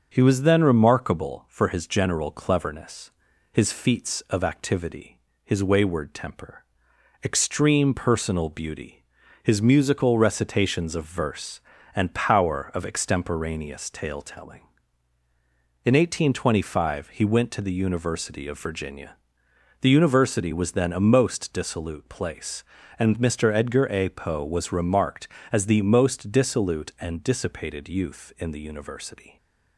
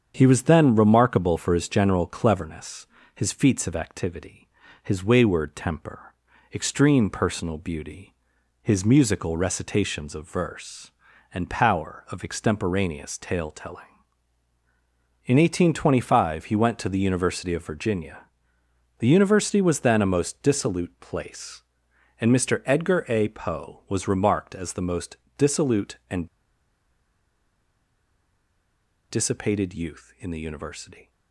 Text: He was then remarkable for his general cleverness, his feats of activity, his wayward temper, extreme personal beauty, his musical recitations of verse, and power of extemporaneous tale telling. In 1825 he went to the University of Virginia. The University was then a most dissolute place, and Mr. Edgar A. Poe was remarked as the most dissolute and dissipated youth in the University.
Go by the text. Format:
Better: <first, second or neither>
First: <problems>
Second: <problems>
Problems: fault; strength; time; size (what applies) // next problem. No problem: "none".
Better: first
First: starts louder than the rest; until 1.1 s; 6.5 dB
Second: starts louder than the rest; strong; until 1.1 s; 7.5 dB // pauses between "most" and "dissolute"; slight; at 25.1 s; 0.18 s long // pauses between "and" and "dissipated"; strong; at 26.2 s; 2.8 s long